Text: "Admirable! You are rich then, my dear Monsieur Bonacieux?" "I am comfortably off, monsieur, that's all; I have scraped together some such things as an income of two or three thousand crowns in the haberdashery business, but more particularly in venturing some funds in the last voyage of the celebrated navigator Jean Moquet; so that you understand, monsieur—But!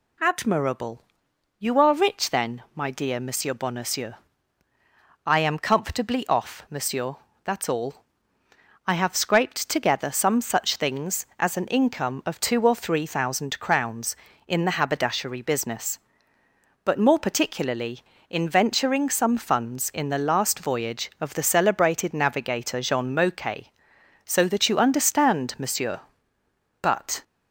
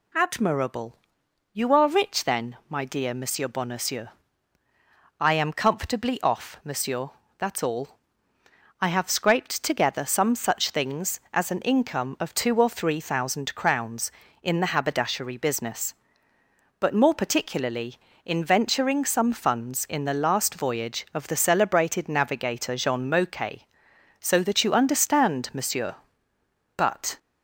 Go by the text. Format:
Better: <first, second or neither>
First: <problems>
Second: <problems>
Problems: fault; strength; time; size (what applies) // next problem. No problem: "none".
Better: neither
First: none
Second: none